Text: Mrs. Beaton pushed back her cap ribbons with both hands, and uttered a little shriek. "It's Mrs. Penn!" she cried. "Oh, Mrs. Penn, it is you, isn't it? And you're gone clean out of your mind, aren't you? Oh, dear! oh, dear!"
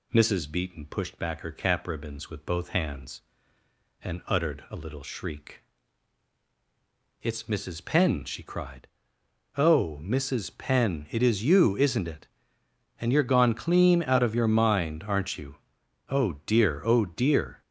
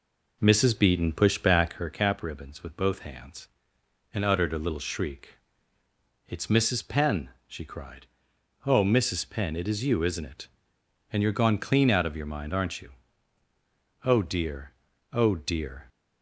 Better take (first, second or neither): first